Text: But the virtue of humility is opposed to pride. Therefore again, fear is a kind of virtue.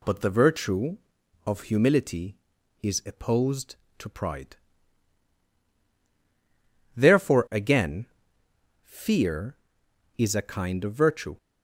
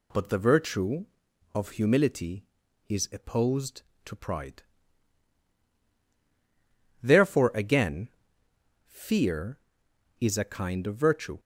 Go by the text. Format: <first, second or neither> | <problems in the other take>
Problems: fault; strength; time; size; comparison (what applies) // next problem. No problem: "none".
neither | none